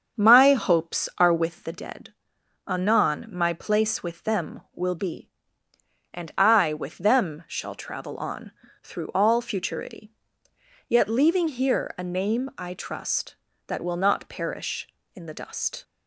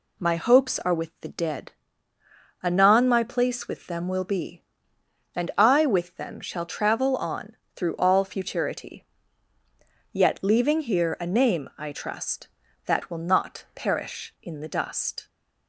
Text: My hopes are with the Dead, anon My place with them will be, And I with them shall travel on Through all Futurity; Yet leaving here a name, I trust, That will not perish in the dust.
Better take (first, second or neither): second